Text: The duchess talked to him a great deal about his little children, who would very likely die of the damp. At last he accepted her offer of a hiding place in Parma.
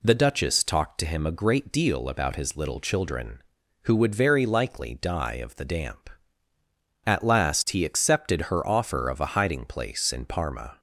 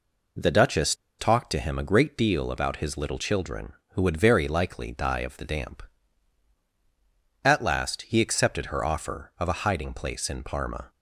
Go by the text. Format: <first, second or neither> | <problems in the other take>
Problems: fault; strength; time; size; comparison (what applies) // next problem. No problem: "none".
first | pauses between "duchess" and "talked"; slight; at 0.9 s; 0.25 s long